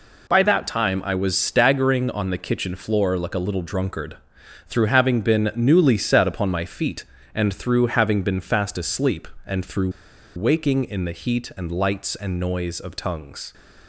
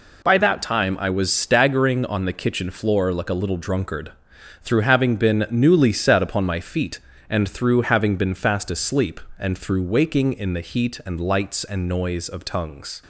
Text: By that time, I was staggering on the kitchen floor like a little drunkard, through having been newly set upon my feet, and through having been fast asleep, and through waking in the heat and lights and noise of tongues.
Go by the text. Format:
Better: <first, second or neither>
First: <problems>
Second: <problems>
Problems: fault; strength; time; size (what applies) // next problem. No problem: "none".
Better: second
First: pauses between "through" and "waking"; noticeable; at 9.8 s; 0.46 s long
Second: none